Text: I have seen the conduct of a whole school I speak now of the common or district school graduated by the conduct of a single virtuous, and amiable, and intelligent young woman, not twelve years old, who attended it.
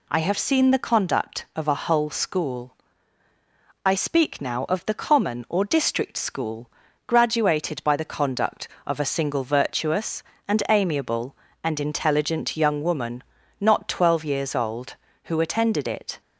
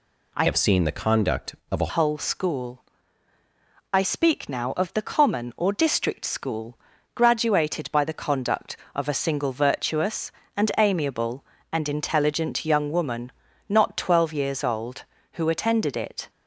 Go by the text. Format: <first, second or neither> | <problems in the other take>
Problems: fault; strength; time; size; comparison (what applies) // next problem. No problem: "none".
first | changes voice from "have" to "a"; from 0.4 to 1.8 s; 1.4 s long // pauses between "school" and "I"; at 2.8 s; 1.1 s long; also in the first // pauses between "school" and "graduated"; at 6.7 s; 0.38 s long; also in the first